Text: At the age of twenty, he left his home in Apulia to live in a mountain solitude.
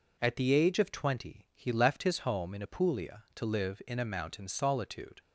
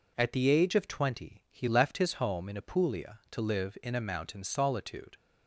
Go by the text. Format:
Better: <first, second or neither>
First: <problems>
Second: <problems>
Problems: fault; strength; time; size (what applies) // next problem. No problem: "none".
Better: neither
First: none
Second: none